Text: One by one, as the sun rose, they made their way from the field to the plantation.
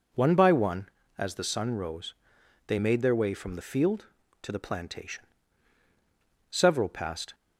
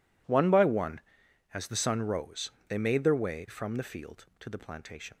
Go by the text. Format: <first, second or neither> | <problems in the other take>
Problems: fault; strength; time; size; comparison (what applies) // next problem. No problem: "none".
second | goes on to say "Several passed"; noticeable; from 6.5 s on; 0.84 s long